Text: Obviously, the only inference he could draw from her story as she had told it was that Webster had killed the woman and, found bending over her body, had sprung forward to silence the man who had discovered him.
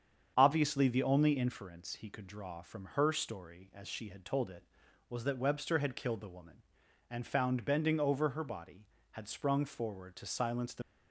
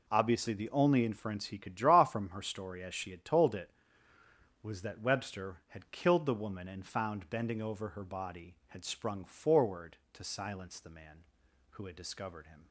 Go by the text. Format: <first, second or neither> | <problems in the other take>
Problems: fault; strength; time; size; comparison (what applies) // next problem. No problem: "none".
second | starts louder than the rest; strong; until 1.3 s; 7.5 dB // stops before "man who had discovered him"; at 10.8 s